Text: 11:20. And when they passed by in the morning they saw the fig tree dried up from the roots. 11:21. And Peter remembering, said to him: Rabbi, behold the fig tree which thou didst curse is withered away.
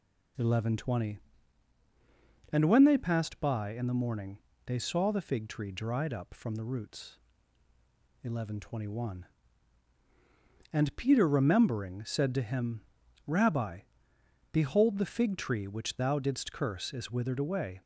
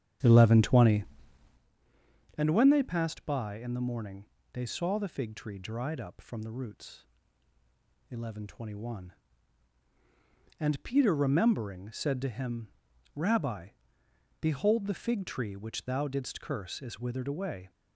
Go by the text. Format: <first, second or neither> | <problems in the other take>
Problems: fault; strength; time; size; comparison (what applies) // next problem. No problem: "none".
first | starts louder than the rest; strong; until 1.7 s; 8.5 dB // pauses between "morning" and "they"; slight; at 4.2 s; 0.26 s long; slight in the first